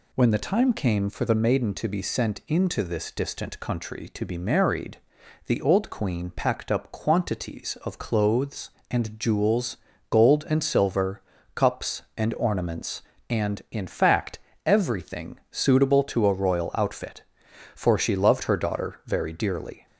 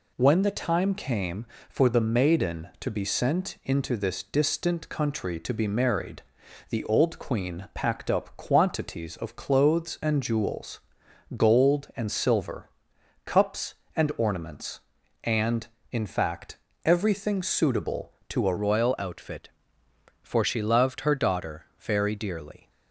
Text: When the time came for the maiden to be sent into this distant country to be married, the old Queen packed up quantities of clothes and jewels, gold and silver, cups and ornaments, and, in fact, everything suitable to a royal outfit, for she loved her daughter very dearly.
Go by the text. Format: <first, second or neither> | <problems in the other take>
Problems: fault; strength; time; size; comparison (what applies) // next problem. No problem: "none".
first | changes voice at "royal"; from 18.5 s on; 4.1 s long